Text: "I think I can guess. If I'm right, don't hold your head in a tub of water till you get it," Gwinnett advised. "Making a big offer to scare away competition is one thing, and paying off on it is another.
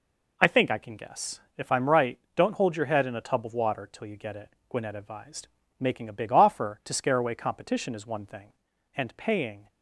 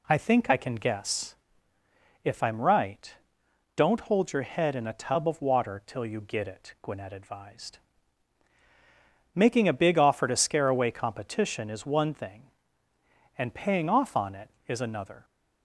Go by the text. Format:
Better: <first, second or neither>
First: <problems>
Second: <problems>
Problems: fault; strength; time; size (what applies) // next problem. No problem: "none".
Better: second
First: stops before "off on it is another"; at 9.6 s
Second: none